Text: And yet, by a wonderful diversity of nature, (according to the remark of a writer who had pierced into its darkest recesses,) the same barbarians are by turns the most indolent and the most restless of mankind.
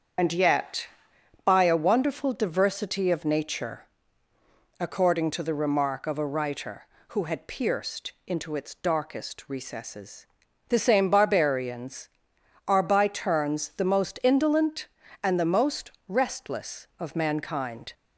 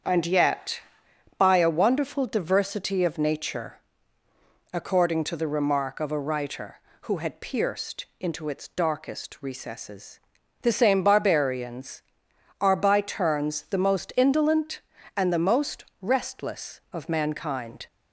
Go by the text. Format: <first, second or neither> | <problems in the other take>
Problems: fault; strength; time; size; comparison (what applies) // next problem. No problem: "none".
second | loses the start of "And"; at 0.1 s; 70 ms // starts louder than the rest; strong; until 1.7 s; 7.5 dB; strong in the second // pauses between "pierced" and "into"; slight; at 8.1 s; 0.16 s long; slight in the second // pauses between "most" and "restless"; slight; at 15.9 s; 0.18 s long; slight in the second